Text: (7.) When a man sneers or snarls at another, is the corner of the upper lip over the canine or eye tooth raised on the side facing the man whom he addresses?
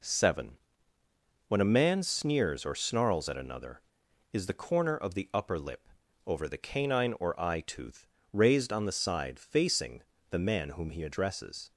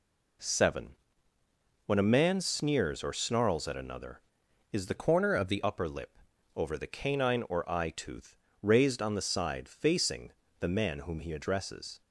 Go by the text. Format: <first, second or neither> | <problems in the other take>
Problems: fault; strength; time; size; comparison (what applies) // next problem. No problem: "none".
first | changes voice from "corner" to "the"; from 4.9 to 5.6 s; 0.7 s long // pauses between "lip" and "over"; slight; at 6.1 s; 0.36 s long; slight in the first // pauses between "tooth" and "raised"; slight; at 8.3 s; 0.24 s long; slight in the first // pauses between "facing" and "the"; slight; at 10.3 s; 0.26 s long; slight in the first